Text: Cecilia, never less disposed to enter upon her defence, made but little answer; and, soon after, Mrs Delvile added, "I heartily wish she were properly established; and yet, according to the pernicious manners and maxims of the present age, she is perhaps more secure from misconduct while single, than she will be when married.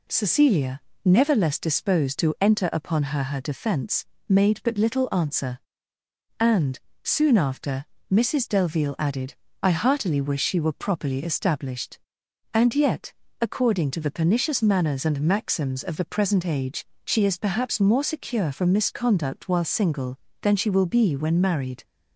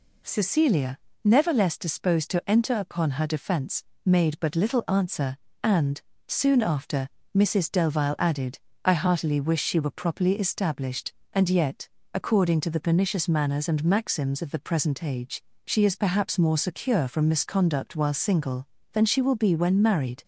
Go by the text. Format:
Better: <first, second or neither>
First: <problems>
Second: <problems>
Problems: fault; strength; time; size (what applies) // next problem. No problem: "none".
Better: second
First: says "her" twice; at 3.2 s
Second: none